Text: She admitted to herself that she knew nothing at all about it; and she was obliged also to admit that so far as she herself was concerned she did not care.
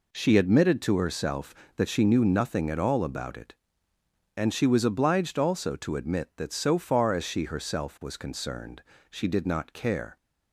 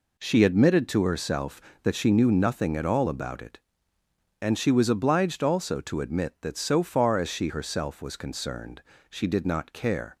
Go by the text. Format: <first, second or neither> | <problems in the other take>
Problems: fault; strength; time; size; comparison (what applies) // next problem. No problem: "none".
neither | pauses between "concerned" and "she"; slight; the same in both